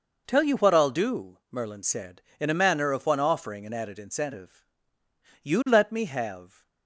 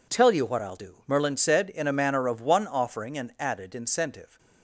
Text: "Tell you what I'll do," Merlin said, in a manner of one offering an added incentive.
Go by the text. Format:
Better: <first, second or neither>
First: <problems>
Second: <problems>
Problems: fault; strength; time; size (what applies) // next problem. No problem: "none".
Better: second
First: goes on to say "You let me have"; noticeable; from 5.4 s on; 1.2 s long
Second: none